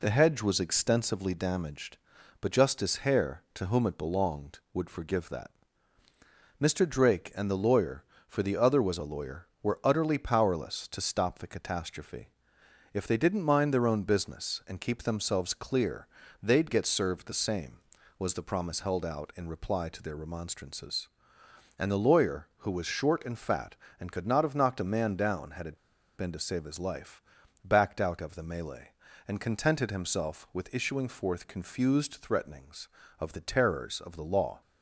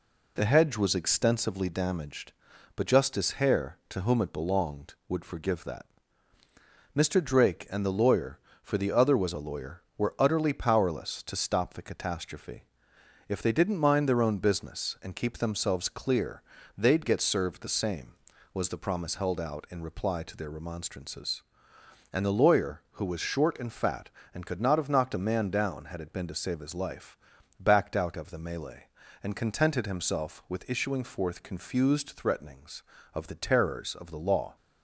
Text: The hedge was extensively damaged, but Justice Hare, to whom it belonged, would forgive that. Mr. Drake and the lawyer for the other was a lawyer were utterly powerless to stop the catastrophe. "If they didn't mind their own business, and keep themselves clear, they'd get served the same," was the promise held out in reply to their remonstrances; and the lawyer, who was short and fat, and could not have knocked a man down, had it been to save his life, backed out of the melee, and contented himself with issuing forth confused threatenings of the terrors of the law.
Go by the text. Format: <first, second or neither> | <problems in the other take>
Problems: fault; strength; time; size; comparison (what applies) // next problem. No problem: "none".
second | pauses between "it" and "been"; at 25.7 s; 0.39 s long